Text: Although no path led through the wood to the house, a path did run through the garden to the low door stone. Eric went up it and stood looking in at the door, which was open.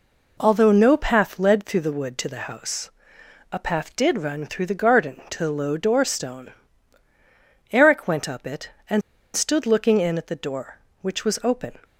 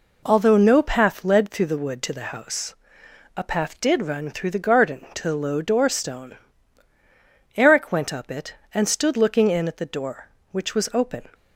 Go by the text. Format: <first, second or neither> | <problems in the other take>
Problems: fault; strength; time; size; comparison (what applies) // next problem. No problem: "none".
second | pauses between "and" and "stood"; slight; at 9.0 s; 0.33 s long